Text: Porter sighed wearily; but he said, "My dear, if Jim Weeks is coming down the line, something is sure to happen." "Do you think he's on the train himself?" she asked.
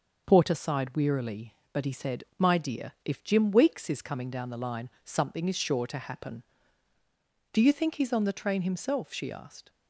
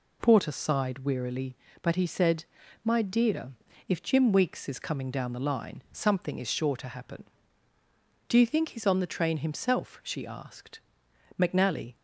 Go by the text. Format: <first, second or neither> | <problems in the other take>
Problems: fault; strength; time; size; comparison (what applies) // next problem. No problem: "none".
first | goes on to say "McNally"; from 11.3 s on; 0.56 s long